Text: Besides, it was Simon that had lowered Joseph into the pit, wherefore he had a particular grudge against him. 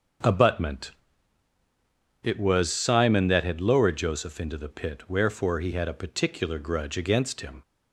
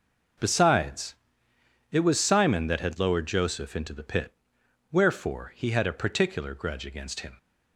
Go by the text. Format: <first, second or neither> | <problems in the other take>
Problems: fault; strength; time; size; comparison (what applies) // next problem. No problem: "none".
second | starts louder than the rest; noticeable; until 2.5 s; 6 dB // says "Abutment" for "Besides"; at 0.2 s